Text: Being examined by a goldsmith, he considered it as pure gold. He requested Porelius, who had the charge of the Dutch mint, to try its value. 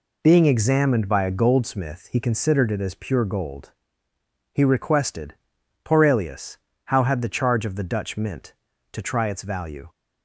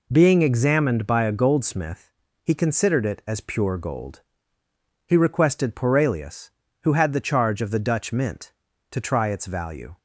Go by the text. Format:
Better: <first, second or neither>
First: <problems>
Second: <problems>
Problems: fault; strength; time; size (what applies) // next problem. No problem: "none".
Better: second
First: pauses between "requested" and "Porelius"; noticeable; at 5.3 s; 0.48 s long // says "how" for "who"; at 6.8 s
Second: none